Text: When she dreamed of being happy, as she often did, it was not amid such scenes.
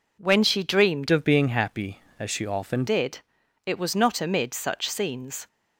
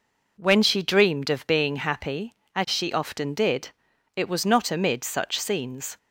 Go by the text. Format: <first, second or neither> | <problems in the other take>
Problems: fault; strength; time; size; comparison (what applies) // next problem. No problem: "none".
second | changes voice from "of" to "often"; from 1.1 to 2.8 s; 1.7 s long